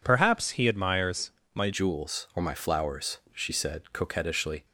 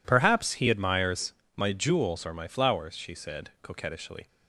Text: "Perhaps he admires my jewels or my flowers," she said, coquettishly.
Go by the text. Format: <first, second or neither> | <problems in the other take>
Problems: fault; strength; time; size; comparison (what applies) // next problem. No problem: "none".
second | pauses between "admires" and "my"; slight; at 1.3 s; 0.22 s long; slight in the second // changes voice at "jewels"; from 1.7 s on; 2.9 s long